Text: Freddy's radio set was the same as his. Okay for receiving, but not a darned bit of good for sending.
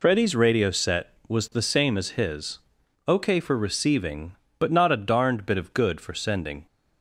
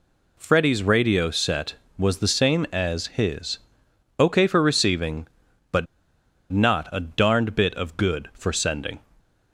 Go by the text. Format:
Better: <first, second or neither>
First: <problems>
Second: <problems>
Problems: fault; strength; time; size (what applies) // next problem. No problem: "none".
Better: first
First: none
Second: pauses between "but" and "not"; noticeable; at 5.8 s; 0.66 s long